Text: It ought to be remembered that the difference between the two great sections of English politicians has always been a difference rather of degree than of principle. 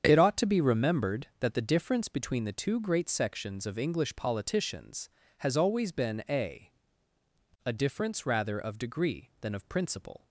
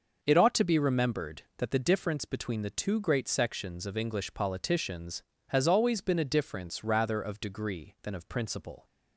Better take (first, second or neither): second